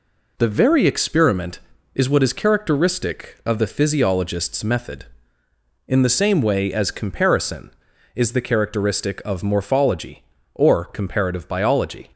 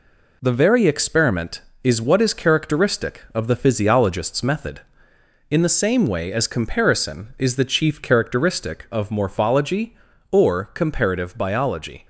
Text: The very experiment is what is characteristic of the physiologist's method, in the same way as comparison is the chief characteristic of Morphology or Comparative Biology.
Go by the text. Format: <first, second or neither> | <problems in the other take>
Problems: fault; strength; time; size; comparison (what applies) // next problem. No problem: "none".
second | skips "chief"; at 8.4 s